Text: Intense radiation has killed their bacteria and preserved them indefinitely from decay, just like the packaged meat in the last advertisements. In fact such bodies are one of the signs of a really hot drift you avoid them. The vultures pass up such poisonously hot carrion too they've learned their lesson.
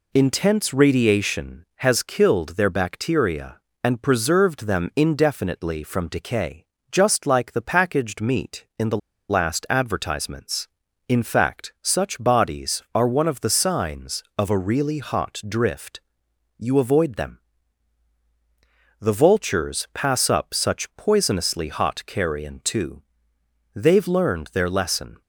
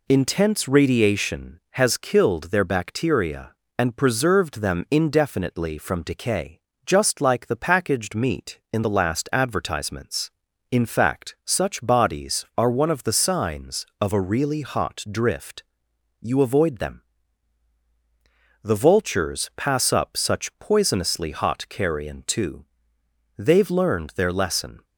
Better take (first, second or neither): second